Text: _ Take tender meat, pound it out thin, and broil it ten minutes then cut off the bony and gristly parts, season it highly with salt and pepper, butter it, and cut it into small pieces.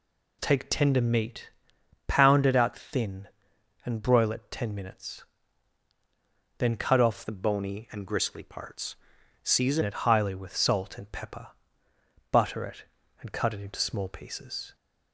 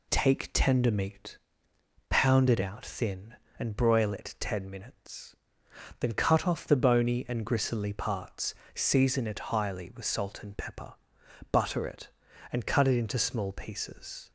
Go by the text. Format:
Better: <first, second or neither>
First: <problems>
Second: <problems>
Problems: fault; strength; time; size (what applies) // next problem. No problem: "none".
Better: second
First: pauses between "minutes" and "then"; strong; at 5.2 s; 1.3 s long // changes voice from "the" to "season"; from 7.2 to 9.8 s; 2.6 s long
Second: pauses between "minutes" and "then"; noticeable; at 5.3 s; 0.66 s long